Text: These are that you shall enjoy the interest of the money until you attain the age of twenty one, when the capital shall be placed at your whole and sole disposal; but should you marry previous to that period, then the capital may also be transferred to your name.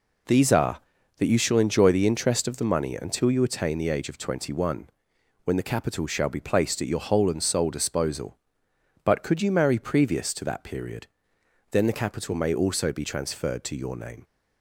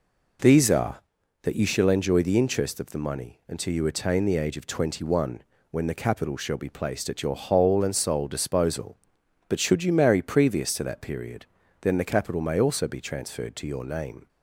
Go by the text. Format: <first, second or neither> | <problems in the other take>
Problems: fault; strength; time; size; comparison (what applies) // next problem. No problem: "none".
second | says "could" for "should"; at 9.2 s